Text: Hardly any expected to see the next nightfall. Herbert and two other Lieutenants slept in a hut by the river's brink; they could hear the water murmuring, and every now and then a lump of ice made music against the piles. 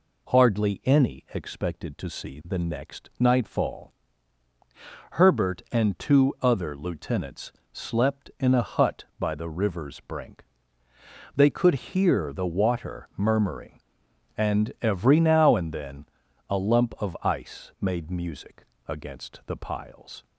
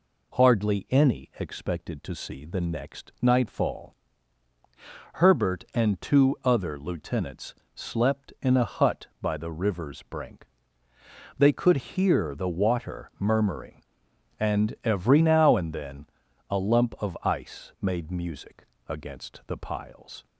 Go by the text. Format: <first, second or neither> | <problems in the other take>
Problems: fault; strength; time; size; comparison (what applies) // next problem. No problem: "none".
neither | pauses between "Lieutenants" and "slept"; slight; the same in both // pauses between "then" and "a"; the same in both // pauses between "music" and "against"; slight; the same in both